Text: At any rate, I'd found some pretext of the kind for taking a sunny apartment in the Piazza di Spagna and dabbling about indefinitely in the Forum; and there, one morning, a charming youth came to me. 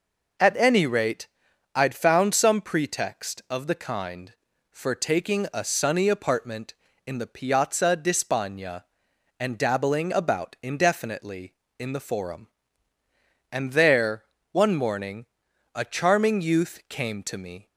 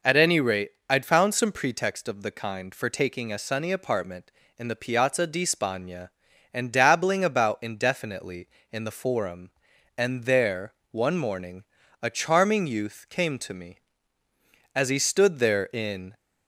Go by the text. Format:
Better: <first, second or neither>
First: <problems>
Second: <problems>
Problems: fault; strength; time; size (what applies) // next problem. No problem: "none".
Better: first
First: none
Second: goes on to say "As he stood there in"; from 14.7 s on; 1.4 s long